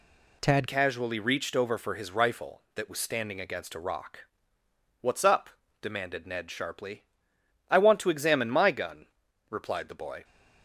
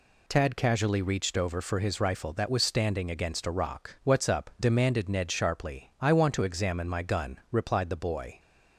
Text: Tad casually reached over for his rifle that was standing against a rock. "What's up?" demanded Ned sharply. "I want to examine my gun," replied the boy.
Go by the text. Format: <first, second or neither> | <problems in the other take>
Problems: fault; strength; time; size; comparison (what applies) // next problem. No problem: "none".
second | changes voice at "casually"; from 0.6 s on; 9.6 s long